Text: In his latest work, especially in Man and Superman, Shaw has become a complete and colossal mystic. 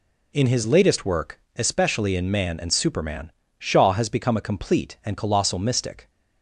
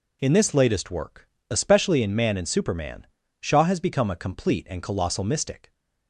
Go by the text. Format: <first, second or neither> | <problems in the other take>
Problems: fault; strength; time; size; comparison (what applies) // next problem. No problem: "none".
first | says "this" for "his"; at 0.3 s